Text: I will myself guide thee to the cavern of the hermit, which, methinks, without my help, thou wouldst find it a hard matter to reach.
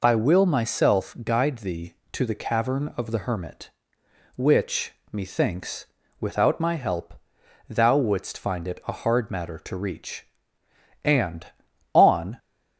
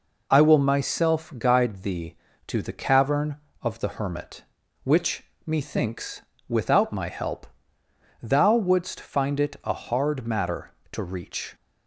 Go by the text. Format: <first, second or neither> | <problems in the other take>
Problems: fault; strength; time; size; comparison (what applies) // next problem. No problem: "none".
second | goes on to say "And on"; from 11.0 s on; 1.3 s long